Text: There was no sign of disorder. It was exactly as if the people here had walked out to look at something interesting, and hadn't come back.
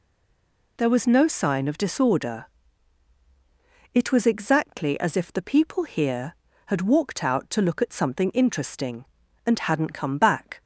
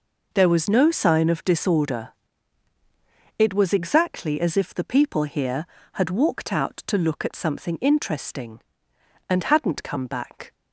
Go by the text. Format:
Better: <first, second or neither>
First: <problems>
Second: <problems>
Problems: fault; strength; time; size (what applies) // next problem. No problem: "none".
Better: second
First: stays silent before the first word; slight; until 0.7 s; 0.7 s long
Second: none